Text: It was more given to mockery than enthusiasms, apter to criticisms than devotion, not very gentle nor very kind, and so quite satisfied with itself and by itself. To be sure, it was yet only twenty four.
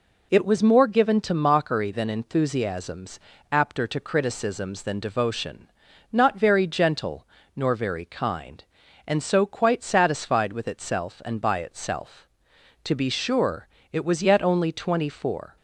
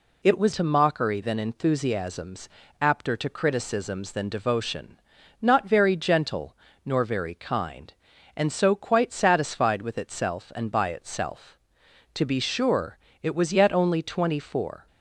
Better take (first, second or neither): first